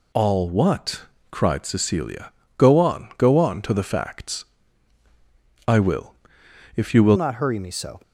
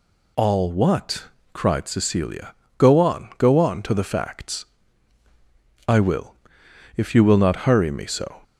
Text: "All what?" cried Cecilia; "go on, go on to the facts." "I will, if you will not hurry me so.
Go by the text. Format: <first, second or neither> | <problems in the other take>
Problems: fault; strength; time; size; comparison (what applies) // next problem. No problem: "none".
second | changes voice at "not"; from 7.1 s on; 0.8 s long